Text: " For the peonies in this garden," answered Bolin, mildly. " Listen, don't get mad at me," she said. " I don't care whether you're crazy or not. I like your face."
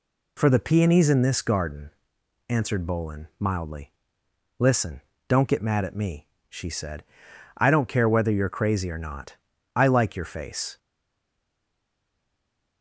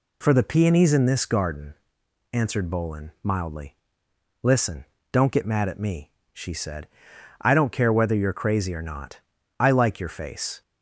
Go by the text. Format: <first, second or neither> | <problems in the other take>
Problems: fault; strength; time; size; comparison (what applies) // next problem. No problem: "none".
second | stays silent after the last word; noticeable; from 10.7 s on; 2.1 s long